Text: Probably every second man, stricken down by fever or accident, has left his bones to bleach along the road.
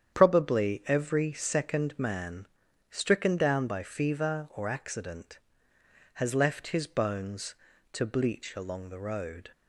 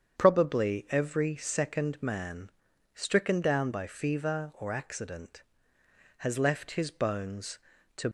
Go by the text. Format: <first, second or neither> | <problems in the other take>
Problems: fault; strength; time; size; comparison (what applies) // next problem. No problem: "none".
first | starts louder than the rest; strong; until 1.2 s; 8 dB; strong in the first // stops before "bleach along the road"; at 8.0 s